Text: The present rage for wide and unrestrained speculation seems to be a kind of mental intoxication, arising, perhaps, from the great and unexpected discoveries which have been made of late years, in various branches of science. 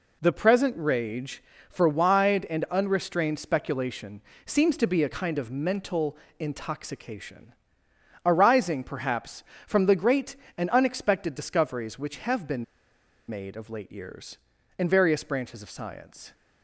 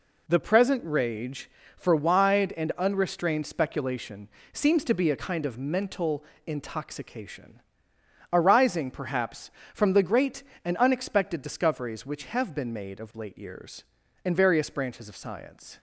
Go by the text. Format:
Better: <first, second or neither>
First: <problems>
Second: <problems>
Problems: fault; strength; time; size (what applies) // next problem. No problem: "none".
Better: second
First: pauses between "speculation" and "seems"; slight; at 4.2 s; 0.24 s long // pauses between "mental" and "intoxication"; slight; at 6.1 s; 0.24 s long // pauses between "been" and "made"; noticeable; at 12.6 s; 0.63 s long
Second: pauses between "speculation" and "seems"; slight; at 4.2 s; 0.24 s long // pauses between "mental" and "intoxication"; slight; at 6.2 s; 0.24 s long